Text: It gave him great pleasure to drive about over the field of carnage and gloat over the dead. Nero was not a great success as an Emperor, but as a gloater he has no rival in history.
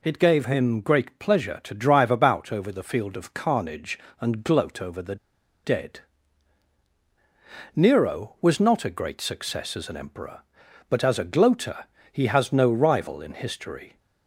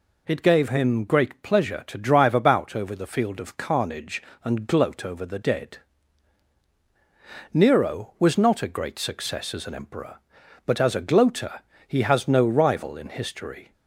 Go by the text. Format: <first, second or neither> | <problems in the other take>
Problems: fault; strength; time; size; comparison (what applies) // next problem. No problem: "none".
second | pauses between "the" and "dead"; noticeable; at 5.1 s; 0.48 s long // pauses between "gloater" and "he"; slight; at 11.8 s; 0.28 s long; slight in the second